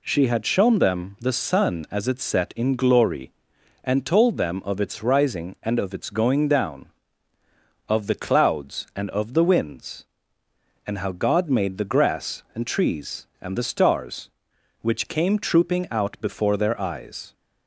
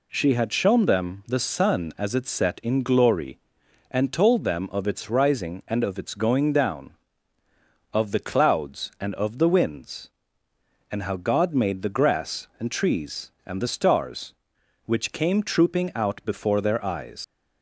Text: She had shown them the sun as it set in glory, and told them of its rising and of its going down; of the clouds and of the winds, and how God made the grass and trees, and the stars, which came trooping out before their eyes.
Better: first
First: none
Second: leaves "eyes" unfinished; at 17.2 s; 125 ms

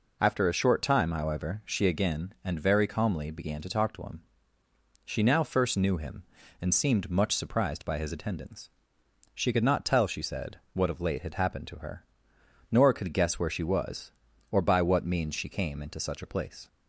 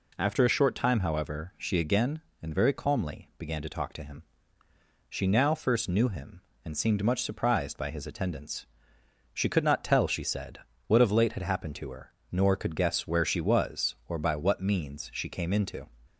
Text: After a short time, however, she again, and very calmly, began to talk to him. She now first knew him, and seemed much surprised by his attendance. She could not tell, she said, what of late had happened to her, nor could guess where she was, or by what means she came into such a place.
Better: first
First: none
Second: stops before "such a place"; at 16.0 s

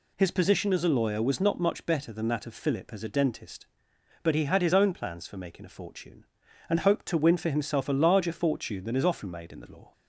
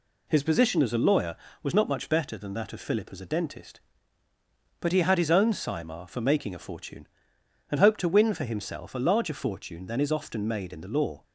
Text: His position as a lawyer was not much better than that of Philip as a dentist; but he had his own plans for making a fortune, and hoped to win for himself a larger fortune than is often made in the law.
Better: first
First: none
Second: says "simar" for "plans"; at 5.5 s

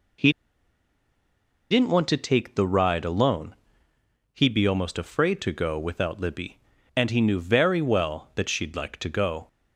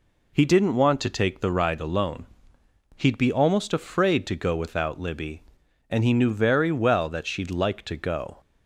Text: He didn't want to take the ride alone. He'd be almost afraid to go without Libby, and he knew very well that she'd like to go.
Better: second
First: pauses between "He" and "didn't"; strong; at 0.3 s; 1.3 s long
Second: none

